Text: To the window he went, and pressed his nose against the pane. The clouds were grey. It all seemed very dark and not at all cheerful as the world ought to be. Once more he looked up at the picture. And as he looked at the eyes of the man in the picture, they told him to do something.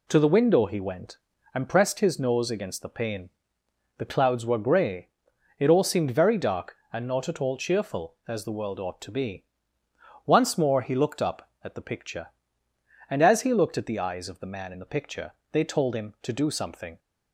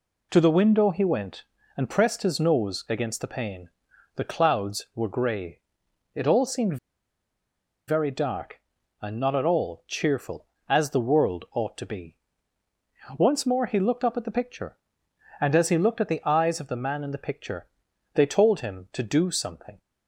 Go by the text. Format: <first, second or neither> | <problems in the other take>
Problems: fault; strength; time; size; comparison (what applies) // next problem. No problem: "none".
first | pauses between "seemed" and "very"; at 6.7 s; 1.1 s long